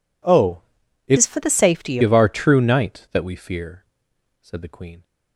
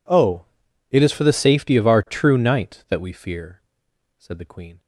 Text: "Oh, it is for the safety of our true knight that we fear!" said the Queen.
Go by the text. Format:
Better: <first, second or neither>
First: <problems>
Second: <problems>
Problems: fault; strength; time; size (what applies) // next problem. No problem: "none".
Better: second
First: changes voice from "is" to "safety"; from 1.1 to 1.9 s; 0.8 s long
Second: none